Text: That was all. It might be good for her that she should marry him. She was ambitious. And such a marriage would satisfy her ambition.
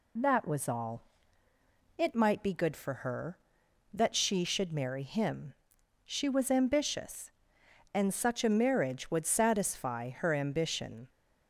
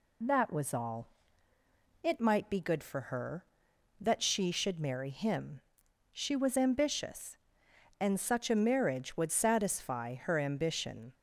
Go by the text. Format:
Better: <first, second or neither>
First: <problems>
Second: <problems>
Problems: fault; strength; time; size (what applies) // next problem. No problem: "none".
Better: neither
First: none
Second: none